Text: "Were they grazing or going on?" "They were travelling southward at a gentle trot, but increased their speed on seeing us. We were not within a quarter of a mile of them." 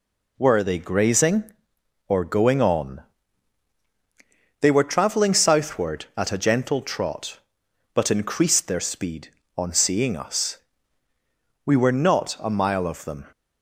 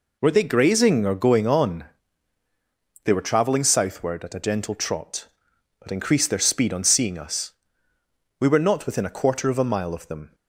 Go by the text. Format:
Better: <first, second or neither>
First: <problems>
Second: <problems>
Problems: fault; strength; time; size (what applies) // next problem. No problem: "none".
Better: second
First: skips "within a quarter of"; at 12.3 s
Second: none